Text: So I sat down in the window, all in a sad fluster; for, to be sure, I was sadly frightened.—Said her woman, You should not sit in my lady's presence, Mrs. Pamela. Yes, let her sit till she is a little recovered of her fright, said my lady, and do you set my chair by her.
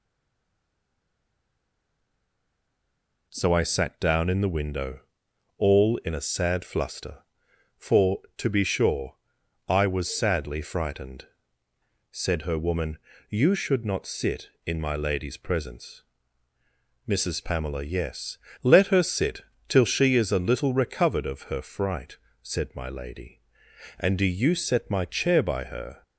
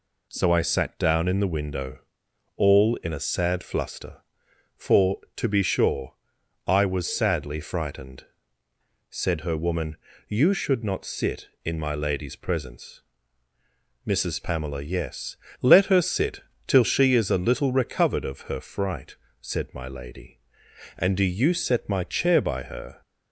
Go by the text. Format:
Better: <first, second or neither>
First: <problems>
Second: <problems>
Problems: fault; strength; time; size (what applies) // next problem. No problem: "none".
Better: second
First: stays silent before the first word; strong; until 3.3 s; 3.3 s long // pauses between "sit" and "till"; slight; at 19.4 s; 0.26 s long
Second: pauses between "sit" and "till"; slight; at 16.4 s; 0.26 s long